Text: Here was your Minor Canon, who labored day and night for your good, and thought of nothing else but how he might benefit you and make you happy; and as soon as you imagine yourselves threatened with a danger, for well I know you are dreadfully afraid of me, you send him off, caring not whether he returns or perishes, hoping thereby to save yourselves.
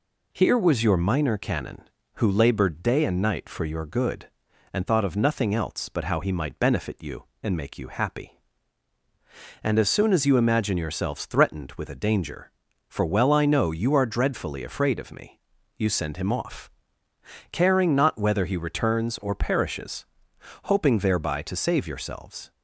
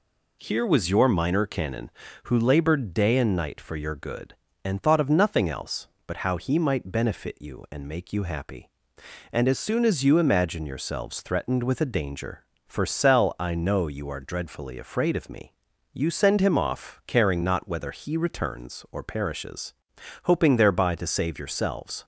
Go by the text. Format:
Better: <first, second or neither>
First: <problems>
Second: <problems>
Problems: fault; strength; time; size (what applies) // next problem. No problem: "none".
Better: first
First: none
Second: says "cell" for "well"; at 12.8 s